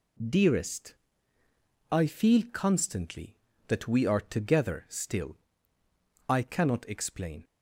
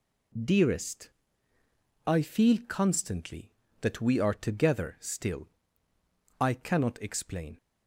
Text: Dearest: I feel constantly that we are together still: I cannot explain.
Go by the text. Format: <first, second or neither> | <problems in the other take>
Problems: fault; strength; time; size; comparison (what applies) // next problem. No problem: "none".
neither | none